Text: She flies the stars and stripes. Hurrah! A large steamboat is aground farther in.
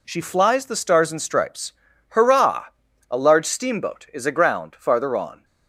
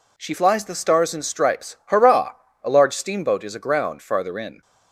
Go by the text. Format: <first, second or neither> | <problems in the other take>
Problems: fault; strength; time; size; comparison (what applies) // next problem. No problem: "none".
second | says "on" for "in"; at 5.1 s